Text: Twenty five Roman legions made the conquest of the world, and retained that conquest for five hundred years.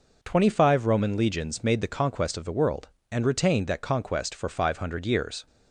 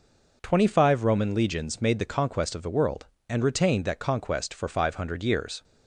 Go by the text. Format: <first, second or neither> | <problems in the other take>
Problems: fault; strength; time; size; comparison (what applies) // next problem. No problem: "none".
neither | none